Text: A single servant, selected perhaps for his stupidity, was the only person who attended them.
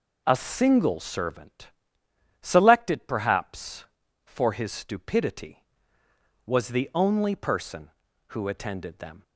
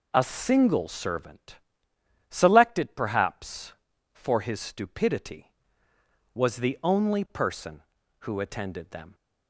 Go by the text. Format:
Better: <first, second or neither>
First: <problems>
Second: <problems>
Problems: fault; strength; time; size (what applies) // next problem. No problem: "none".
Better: neither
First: none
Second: none